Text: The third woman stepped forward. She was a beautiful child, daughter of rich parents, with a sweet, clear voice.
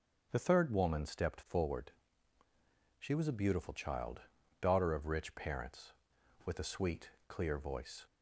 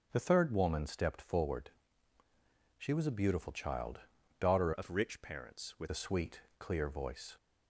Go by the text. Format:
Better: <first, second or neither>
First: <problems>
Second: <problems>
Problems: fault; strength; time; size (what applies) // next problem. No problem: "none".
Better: first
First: starts louder than the rest; strong; until 1.3 s; 7.5 dB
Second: starts louder than the rest; strong; until 1.1 s; 7 dB // changes voice from "of" to "with"; from 4.7 to 5.8 s; 1.1 s long